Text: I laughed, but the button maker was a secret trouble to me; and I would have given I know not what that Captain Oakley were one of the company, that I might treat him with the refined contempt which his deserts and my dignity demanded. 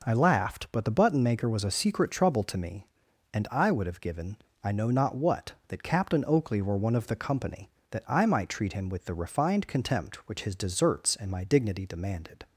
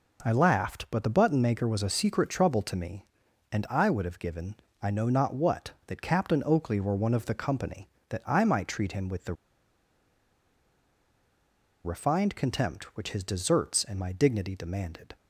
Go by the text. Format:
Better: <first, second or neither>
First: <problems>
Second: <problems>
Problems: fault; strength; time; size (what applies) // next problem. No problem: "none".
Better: first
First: pauses between "given" and "I"; slight; at 4.3 s; 0.28 s long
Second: pauses between "given" and "I"; slight; at 4.5 s; 0.28 s long // pauses between "the" and "refined"; strong; at 9.3 s; 2.5 s long